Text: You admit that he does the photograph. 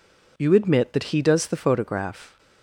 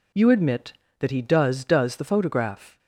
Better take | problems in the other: first | says "does" twice; at 1.6 s

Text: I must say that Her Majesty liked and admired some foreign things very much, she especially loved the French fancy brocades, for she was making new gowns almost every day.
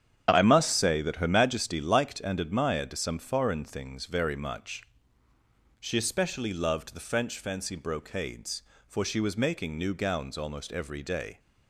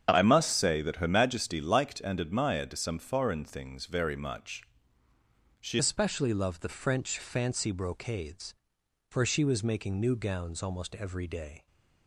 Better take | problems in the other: first | starts louder than the rest; strong; until 1.1 s; 7.5 dB; strong in the first // changes voice at "especially"; from 5.7 s on; 5.9 s long

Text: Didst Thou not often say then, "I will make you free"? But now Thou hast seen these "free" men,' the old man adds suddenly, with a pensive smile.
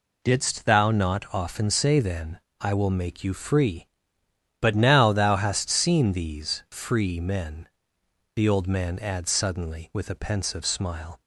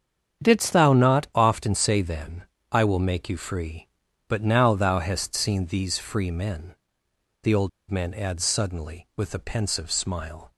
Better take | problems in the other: first | starts louder than the rest; strong; until 1.4 s; 8 dB // pauses between "old" and "man"; slight; at 7.6 s; 0.20 s long

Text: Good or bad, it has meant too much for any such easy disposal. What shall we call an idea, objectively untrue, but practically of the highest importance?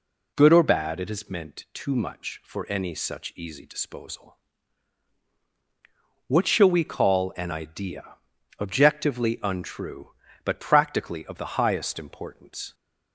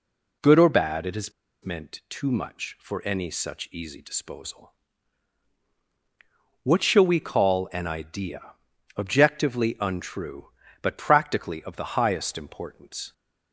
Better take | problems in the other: first | pauses between "has" and "meant"; slight; at 1.3 s; 0.32 s long

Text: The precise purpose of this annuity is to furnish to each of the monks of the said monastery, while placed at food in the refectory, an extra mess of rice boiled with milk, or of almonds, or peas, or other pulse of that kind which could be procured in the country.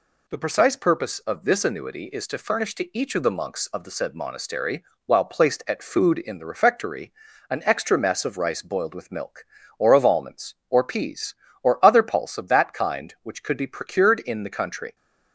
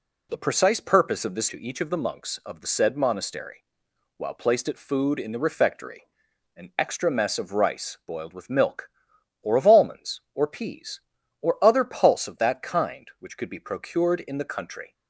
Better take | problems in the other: first | skips "annuity is to furnish"; at 1.4 s

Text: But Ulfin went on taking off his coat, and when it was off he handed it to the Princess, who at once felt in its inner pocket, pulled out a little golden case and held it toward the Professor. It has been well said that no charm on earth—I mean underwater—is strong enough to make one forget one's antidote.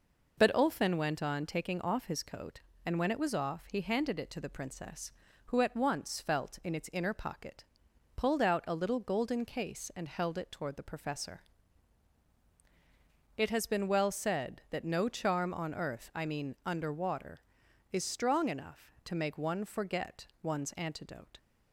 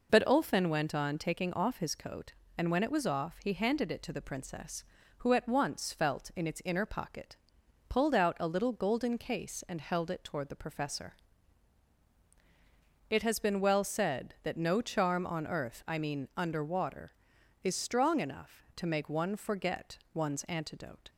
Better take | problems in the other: neither | pauses between "forget" and "one's"; slight; the same in both

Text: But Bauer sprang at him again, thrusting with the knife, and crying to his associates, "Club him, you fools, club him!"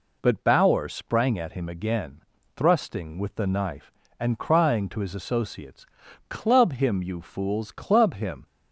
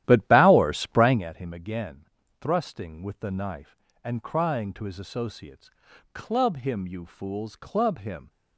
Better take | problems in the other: first | starts louder than the rest; strong; until 1.2 s; 12.5 dB

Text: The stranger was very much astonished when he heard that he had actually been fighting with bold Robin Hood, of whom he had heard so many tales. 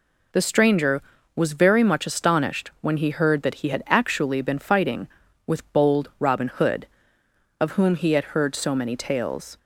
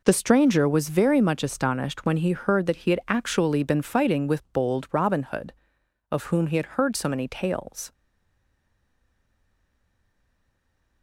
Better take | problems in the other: first | stays silent after the last word; strong; from 7.9 s on; 3.1 s long

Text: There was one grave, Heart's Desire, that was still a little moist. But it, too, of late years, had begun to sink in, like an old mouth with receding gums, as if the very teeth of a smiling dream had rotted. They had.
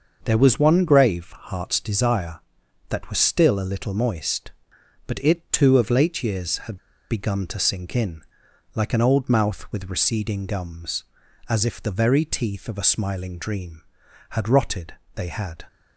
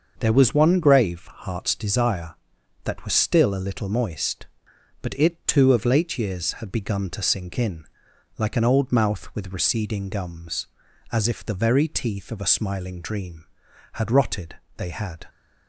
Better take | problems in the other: second | starts louder than the rest; until 1.2 s; 6 dB; also in the second // pauses between "had" and "begun"; slight; at 6.7 s; 0.32 s long

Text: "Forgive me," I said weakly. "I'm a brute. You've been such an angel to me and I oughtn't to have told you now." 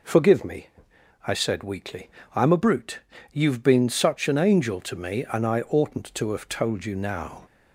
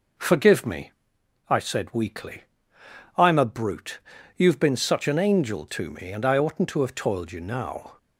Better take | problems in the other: first | says "toiled" for "told"; at 6.9 s

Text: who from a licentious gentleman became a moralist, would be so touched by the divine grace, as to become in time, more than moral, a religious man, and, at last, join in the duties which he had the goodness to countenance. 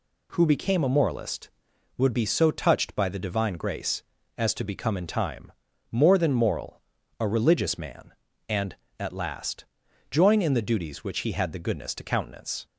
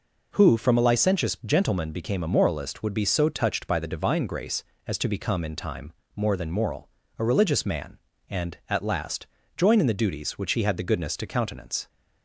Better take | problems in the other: second | skips "from a licentious gentleman"; at 0.4 s

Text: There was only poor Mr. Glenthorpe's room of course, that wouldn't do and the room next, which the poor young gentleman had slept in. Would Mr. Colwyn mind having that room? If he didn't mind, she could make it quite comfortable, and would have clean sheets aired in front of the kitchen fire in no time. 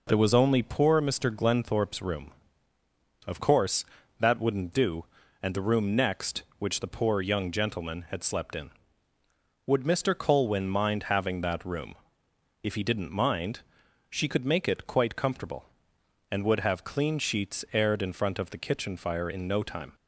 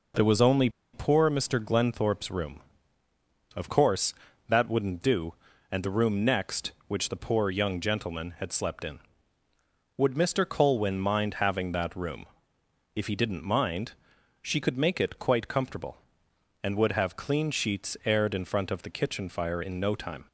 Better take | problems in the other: first | pauses between "only" and "poor"; slight; at 0.6 s; 0.24 s long

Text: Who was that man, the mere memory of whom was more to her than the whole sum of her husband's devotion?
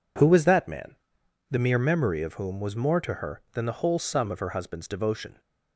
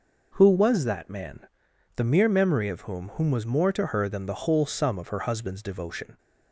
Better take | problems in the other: first | says "whom" twice; at 3.1 s

